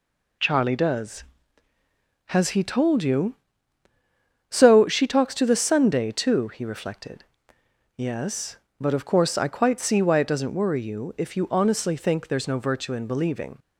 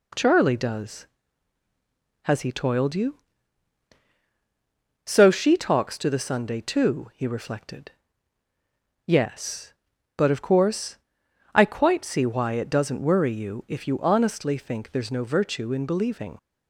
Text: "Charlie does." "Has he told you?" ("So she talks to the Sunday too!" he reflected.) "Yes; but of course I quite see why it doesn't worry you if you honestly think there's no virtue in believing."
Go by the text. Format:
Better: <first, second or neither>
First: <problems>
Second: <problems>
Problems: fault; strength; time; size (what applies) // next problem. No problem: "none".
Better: first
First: none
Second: says "toiled" for "told"; at 2.5 s // pauses between "course" and "I"; noticeable; at 10.9 s; 0.58 s long